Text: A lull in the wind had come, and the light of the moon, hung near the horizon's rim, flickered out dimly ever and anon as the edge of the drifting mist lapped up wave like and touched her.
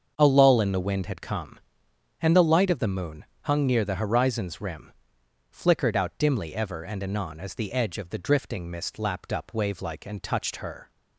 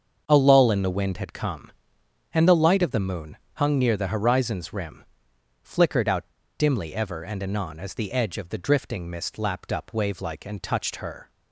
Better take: first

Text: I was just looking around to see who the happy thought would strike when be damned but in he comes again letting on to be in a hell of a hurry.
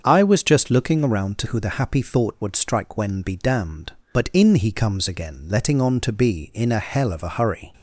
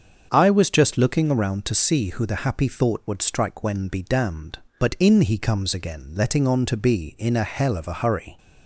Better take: second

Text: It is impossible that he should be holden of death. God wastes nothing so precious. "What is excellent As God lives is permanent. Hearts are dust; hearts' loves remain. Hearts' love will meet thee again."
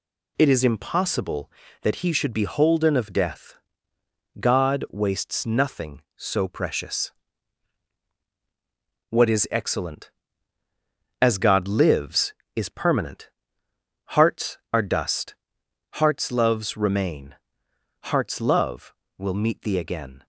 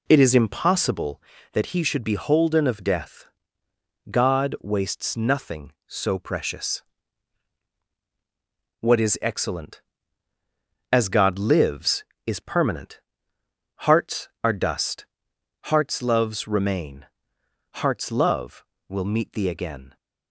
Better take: first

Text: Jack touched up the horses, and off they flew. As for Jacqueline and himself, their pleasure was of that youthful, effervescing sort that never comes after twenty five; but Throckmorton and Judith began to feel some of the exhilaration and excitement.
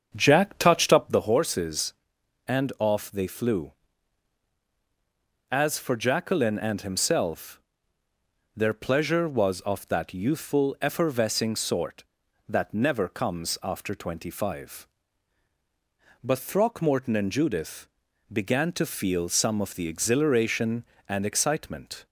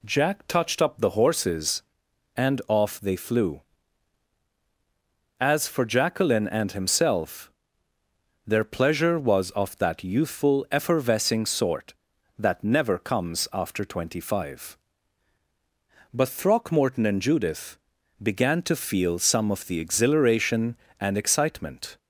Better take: second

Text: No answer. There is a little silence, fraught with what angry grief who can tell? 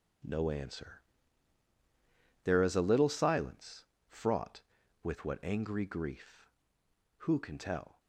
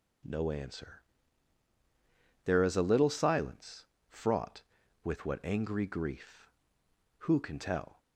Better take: second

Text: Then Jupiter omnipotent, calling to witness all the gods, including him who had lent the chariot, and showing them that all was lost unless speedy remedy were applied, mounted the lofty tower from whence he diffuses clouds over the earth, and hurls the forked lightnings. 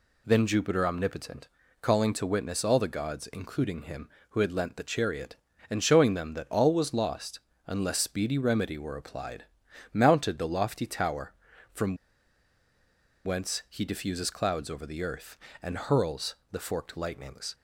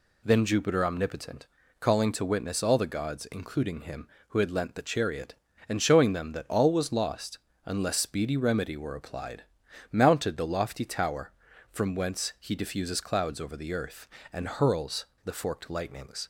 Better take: second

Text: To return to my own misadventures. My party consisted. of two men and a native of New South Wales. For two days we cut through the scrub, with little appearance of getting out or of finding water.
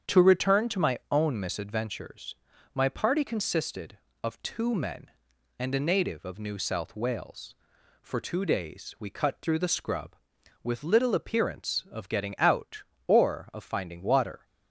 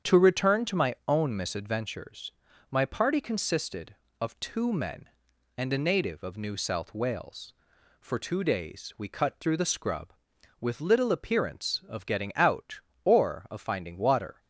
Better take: neither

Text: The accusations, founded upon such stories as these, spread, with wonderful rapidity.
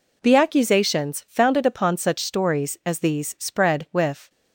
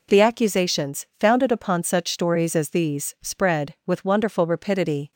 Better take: second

